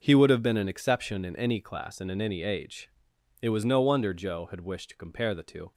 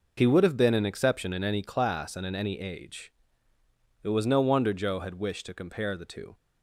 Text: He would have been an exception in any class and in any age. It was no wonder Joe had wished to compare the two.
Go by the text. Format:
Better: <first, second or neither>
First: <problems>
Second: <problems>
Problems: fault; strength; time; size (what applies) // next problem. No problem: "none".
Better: neither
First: none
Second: none